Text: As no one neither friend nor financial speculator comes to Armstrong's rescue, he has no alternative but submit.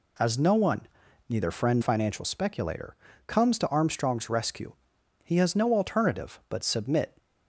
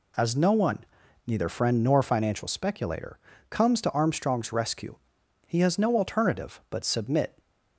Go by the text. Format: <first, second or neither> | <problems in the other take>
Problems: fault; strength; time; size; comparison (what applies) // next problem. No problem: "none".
second | pauses between "one" and "neither"; noticeable; at 0.8 s; 0.48 s long; noticeable in the second // skips "nor"; at 1.8 s // pauses between "speculator" and "comes"; slight; at 2.9 s; 0.32 s long; slight in the second